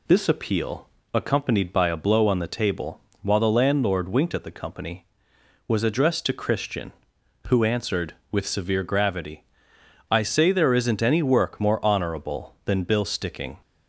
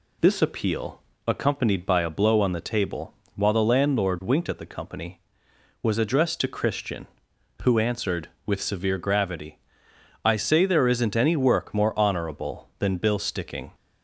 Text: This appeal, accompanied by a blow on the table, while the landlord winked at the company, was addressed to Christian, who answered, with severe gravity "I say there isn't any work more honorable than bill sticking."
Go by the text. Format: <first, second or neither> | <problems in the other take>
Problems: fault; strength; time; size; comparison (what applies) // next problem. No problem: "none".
neither | pauses between "gravity" and "I"; noticeable; the same in both